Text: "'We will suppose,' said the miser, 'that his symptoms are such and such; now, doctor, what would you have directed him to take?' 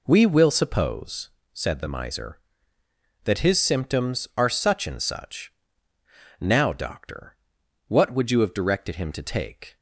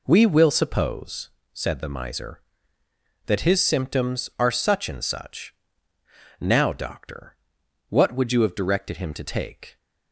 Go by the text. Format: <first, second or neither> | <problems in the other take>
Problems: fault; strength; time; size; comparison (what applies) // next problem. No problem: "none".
neither | none